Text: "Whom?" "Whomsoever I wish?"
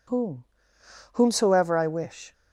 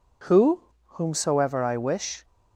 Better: first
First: none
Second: says "Who" for "Whom"; at 0.2 s

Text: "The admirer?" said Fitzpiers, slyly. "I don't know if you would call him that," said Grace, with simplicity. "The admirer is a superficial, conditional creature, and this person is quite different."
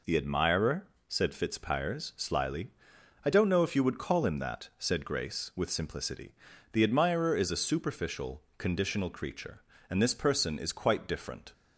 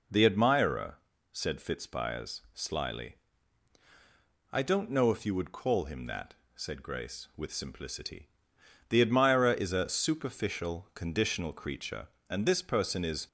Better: first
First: none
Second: stops before "quite different"; at 13.2 s

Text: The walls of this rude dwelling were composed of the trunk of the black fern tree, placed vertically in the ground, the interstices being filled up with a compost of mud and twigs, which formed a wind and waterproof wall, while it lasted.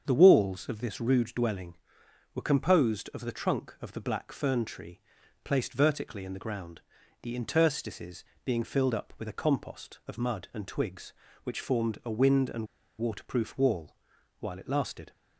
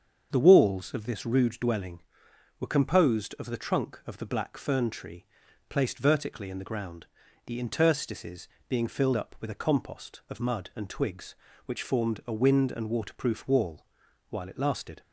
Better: second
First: starts louder than the rest; until 1.0 s; 7 dB // pauses between "interstices" and "being"; slight; at 8.2 s; 0.22 s long // pauses between "and" and "waterproof"; slight; at 12.6 s; 0.32 s long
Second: starts louder than the rest; until 1.3 s; 7 dB // pauses between "interstices" and "being"; slight; at 8.4 s; 0.22 s long

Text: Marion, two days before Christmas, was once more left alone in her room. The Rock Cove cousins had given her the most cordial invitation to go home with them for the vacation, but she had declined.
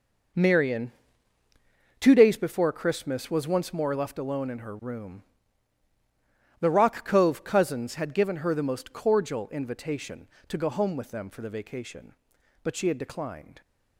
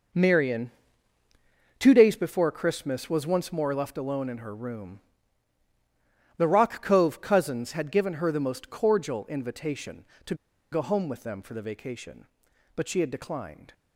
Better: first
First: none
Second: pauses between "to" and "go"; at 10.3 s; 0.37 s long

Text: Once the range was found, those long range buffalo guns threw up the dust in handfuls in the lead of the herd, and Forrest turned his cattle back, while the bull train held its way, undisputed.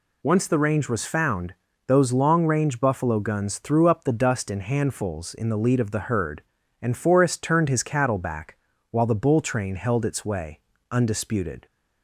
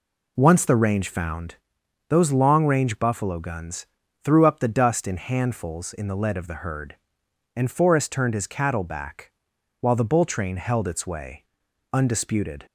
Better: first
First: none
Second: skips "was"; at 1.0 s // pauses between "guns" and "threw"; slight; at 3.8 s; 0.36 s long

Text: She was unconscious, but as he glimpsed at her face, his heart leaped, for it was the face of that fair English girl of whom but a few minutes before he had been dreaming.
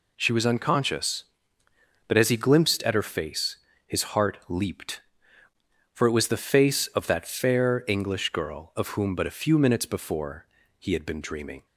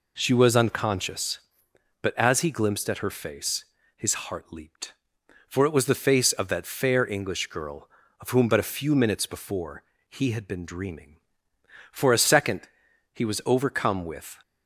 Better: first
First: pauses between "before" and "he"; slight; at 10.4 s; 0.34 s long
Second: pauses between "before" and "he"; slight; at 9.8 s; 0.26 s long // goes on to say "For a second he was overcome with"; strong; from 11.9 s on; 2.4 s long

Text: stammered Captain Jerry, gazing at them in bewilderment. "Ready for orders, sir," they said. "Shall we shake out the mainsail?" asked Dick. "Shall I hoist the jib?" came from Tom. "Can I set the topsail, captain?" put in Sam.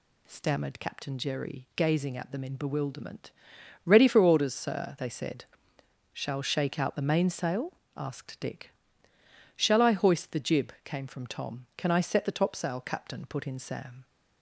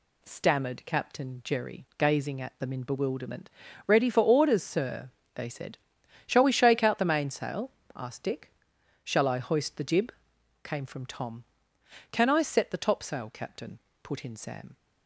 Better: second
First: skips "we"; at 6.4 s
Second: none

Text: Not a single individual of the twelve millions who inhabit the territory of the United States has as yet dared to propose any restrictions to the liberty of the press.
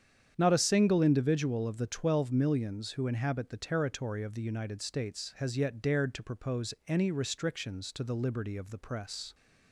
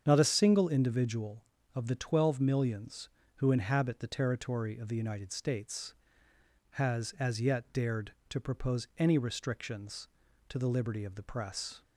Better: second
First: starts louder than the rest; strong; until 1.3 s; 8.5 dB // skips "as"; at 5.5 s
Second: starts louder than the rest; strong; until 1.0 s; 7.5 dB

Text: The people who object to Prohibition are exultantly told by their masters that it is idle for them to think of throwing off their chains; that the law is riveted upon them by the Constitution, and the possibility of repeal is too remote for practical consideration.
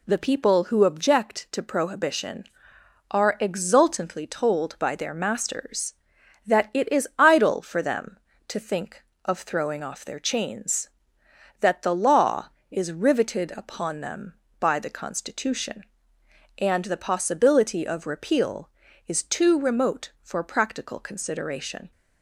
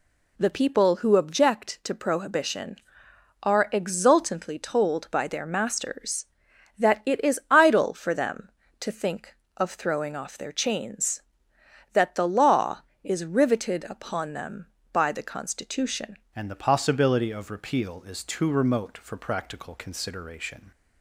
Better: first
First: none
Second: changes voice at "and"; from 16.3 s on; 4.4 s long

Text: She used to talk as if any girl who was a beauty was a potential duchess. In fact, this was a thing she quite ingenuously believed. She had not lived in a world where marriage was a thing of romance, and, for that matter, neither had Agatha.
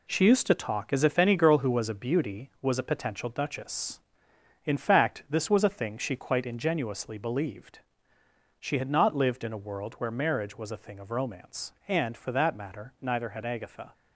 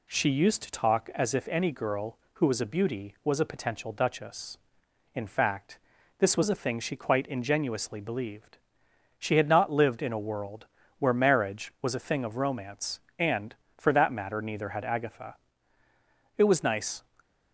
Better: first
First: none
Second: pauses between "world" and "where"; slight; at 10.6 s; 0.32 s long // goes on to say "It was nice"; noticeable; from 16.3 s on; 0.66 s long

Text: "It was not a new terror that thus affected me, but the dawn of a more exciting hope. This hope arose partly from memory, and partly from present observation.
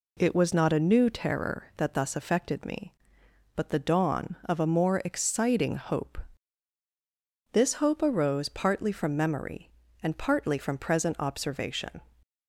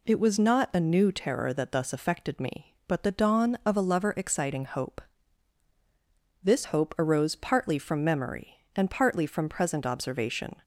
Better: first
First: none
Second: says "lover" for "more"; at 3.8 s

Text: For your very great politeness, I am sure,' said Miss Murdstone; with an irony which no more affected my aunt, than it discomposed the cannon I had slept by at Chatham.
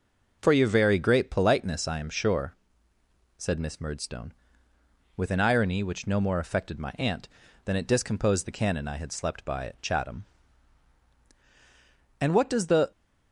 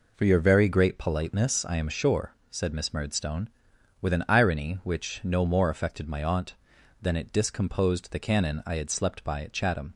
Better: second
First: goes on to say "And what does the"; noticeable; from 12.2 s on; 0.70 s long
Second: none

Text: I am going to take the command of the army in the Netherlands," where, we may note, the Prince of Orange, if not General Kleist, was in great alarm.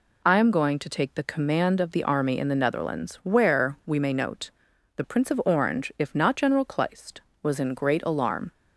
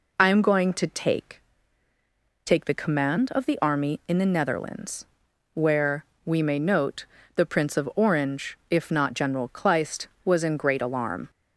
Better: first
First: none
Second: says "take" twice; at 2.4 s

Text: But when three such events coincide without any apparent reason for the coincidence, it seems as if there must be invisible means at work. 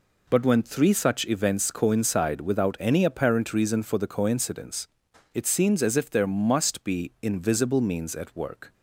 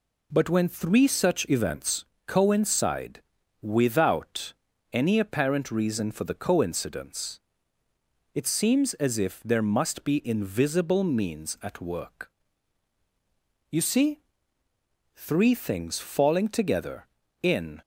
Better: first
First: none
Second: pauses between "events" and "coincide"; slight; at 2.0 s; 0.20 s long // pauses between "coincide" and "without"; at 3.2 s; 0.40 s long // pauses between "without" and "any"; at 4.5 s; 0.40 s long // goes on to say "You see three things falling together in"; strong; from 13.6 s on; 4.1 s long

